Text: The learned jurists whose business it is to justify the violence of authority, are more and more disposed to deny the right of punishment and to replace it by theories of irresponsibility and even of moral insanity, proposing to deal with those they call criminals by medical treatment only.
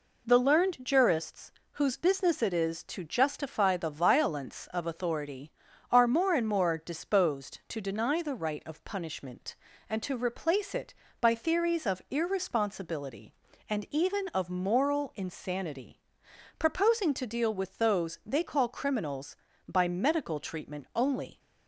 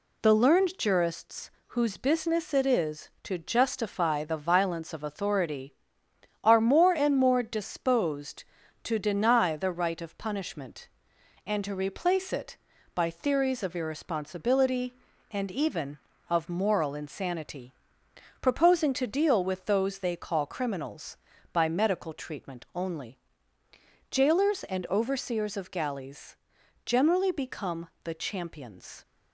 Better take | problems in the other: first | pauses between "jurists" and "whose"; slight; at 1.4 s; 0.20 s long; slight in the first // goes on to say "Jailers and overseers of galleys generally become the champions"; strong; from 24.1 s on; 4.9 s long

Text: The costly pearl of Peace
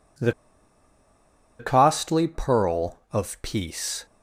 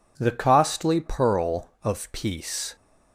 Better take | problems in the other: second | pauses between "The" and "costly"; strong; at 0.3 s; 1.2 s long

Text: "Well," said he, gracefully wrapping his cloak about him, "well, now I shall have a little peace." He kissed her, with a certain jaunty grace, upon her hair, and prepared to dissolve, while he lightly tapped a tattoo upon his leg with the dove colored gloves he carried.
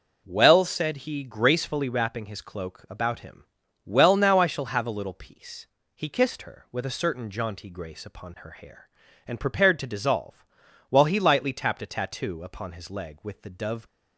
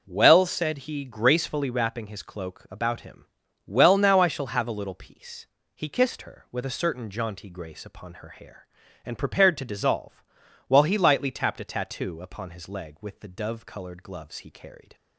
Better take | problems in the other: second | stops before "colored gloves he carried"; at 13.8 s

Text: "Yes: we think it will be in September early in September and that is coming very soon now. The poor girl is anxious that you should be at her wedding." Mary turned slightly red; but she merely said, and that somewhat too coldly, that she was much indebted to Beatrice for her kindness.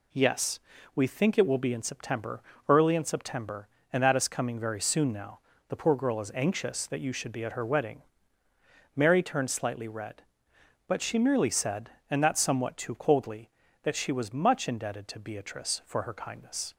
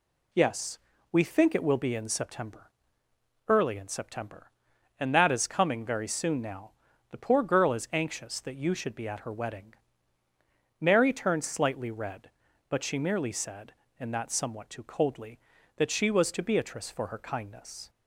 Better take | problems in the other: first | pauses between "September" and "early"; noticeable; at 2.6 s; 0.78 s long; slight in the first // skips "much indebted"; at 16.3 s

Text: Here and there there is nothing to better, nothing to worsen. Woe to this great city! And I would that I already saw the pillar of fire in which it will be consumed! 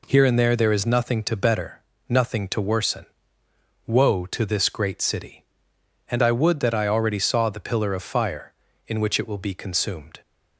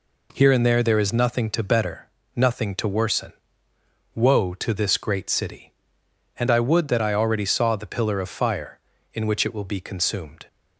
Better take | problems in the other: neither | none

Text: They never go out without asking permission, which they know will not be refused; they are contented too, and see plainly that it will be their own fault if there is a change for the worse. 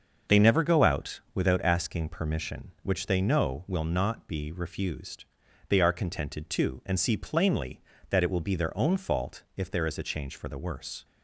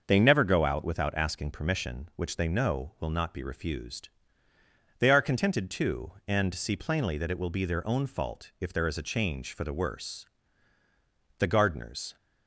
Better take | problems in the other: first | starts louder than the rest; until 1.0 s; 6 dB; also in the first // goes on to say "The gardeners"; noticeable; from 11.3 s on; 0.78 s long

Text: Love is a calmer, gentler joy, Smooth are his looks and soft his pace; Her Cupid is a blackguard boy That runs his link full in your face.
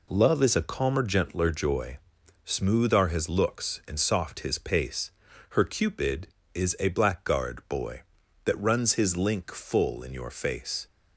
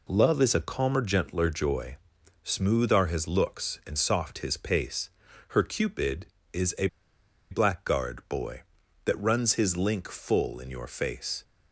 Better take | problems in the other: first | pauses between "a" and "blackguard"; noticeable; at 6.8 s; 0.63 s long

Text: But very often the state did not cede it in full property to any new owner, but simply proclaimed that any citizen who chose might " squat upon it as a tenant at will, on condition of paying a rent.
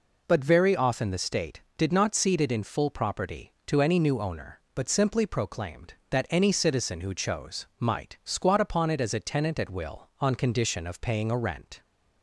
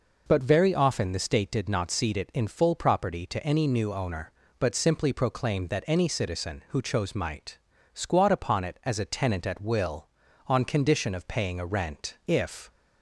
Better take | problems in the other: first | goes on to say "If"; slight; from 12.2 s on; 0.42 s long

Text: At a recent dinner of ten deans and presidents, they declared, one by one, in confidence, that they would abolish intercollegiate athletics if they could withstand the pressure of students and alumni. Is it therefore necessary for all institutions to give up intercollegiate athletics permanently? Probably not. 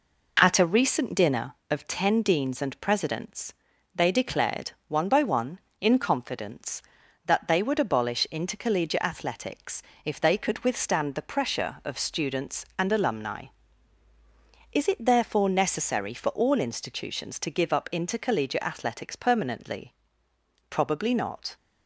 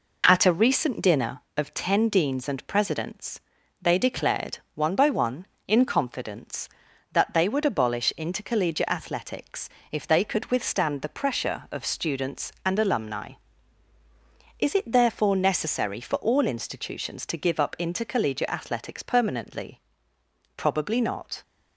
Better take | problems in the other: neither | pauses between "athletics" and "if"; slight; the same in both

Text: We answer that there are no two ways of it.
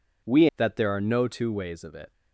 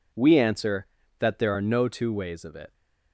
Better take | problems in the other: second | skips "answer"; at 0.5 s

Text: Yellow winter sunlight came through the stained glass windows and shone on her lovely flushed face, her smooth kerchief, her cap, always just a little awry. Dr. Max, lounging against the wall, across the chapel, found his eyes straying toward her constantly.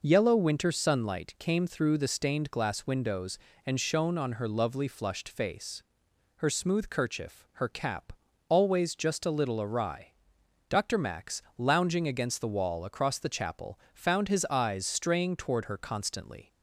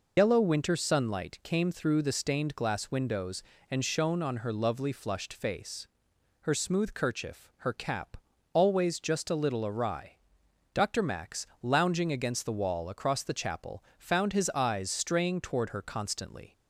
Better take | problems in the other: first | loses the start of "Yellow"; at 0.1 s; 90 ms

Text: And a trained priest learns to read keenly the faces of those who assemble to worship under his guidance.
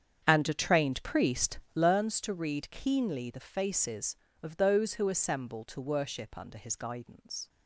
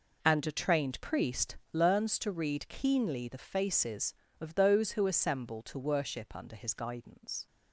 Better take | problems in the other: second | starts louder than the rest; strong; until 2.0 s; 8 dB // pauses between "priest" and "learns"; slight; at 1.5 s; 0.16 s long; slight in the second

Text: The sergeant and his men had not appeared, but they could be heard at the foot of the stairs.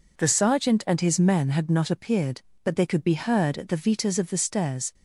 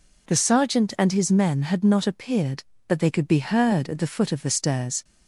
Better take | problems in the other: second | says "vitas" for "foot"; at 3.7 s

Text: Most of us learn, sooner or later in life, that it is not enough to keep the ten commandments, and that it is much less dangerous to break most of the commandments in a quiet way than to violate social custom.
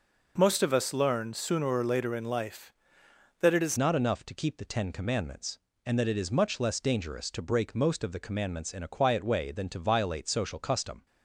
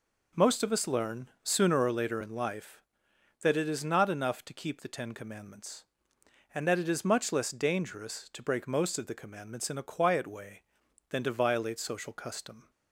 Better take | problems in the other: second | changes voice at "not"; from 3.7 s on; 7.3 s long

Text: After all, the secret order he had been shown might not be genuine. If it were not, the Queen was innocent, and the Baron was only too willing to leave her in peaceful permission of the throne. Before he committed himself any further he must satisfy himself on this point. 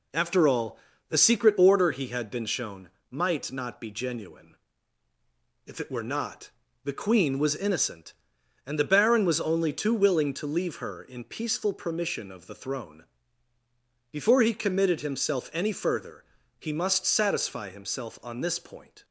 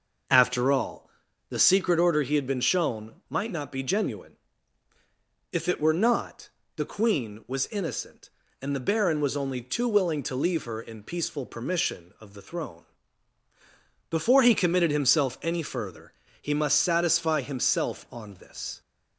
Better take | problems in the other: first | pauses between "shown" and "might"; slight; at 3.1 s; 0.16 s long; slight in the first // pauses between "further" and "he"; slight; at 16.1 s; 0.28 s long; slight in the first // stops before "point"; at 18.8 s

